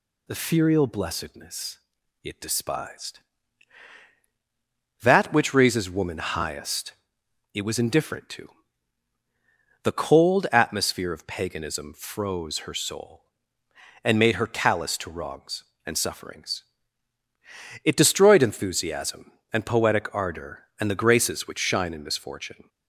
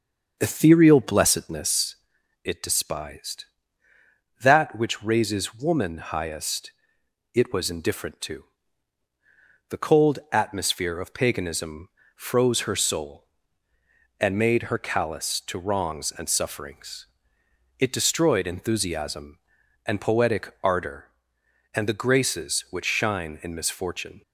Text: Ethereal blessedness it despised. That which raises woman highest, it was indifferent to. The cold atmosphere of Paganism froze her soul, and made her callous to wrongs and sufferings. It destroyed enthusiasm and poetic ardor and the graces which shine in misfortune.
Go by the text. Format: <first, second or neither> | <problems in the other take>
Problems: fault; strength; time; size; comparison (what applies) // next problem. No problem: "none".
first | starts louder than the rest; until 2.1 s; 6.5 dB // pauses between "blessedness" and "it"; noticeable; at 1.9 s; 0.48 s long; also in the first // pauses between "Paganism" and "froze"; slight; at 11.8 s; 0.28 s long